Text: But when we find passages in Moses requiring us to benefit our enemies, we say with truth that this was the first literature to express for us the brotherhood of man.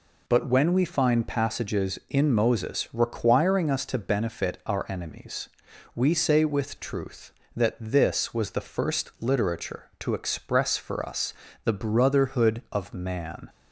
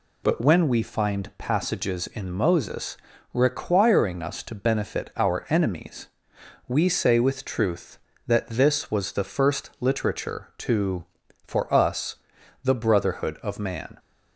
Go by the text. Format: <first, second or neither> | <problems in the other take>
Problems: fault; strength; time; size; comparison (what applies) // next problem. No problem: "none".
first | pauses between "Moses" and "requiring"; at 2.9 s; 0.38 s long // skips "express"; at 11.2 s // pauses between "us" and "the"; noticeable; at 12.1 s; 0.48 s long; slight in the first